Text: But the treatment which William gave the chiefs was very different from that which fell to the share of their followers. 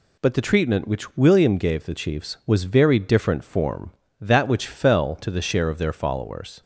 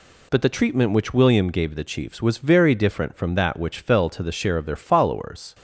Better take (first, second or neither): second